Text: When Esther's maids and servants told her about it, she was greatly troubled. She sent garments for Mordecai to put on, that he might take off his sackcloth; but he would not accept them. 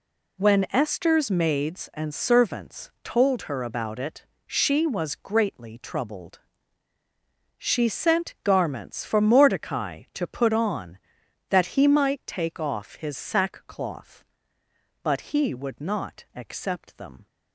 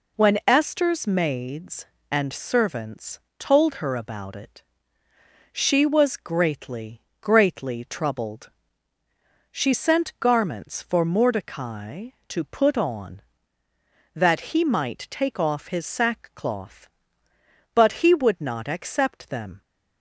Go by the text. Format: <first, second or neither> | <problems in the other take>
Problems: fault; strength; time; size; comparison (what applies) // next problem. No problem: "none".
first | pauses between "servants" and "told"; slight; at 3.1 s; 0.22 s long // says "greatly" twice; at 7.1 s